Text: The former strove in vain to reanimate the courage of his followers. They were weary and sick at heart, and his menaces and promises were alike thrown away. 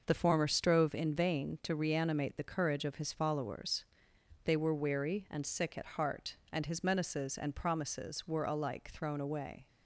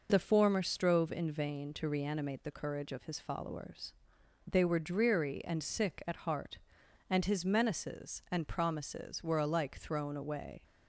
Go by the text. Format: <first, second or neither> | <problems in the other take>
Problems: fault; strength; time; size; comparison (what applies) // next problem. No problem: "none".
first | says "dreary" for "weary"; at 4.8 s